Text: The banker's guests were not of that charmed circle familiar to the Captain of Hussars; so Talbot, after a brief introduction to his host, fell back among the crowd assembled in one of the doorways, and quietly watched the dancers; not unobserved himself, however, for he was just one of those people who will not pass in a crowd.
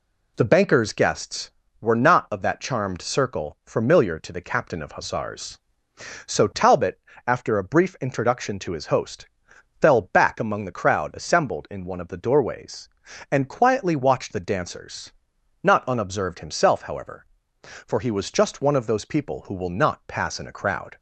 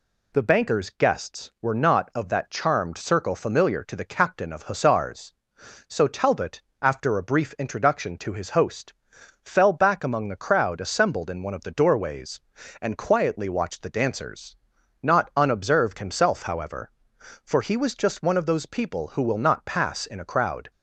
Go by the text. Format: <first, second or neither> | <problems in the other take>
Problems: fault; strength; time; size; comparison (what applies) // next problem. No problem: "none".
neither | none